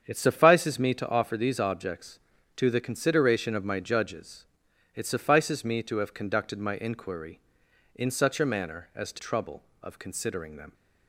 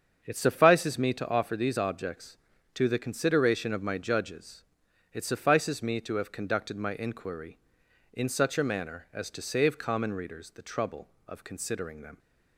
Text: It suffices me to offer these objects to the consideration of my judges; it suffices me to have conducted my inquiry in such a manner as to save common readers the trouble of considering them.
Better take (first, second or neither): second